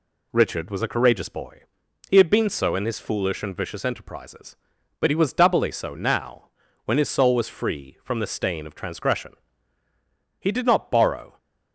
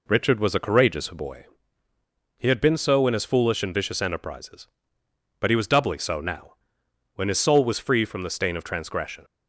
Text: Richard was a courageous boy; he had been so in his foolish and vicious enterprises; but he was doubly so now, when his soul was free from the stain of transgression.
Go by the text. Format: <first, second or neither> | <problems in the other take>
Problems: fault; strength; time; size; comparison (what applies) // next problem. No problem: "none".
second | goes on to say "He did not borrow"; noticeable; from 10.3 s on; 0.98 s long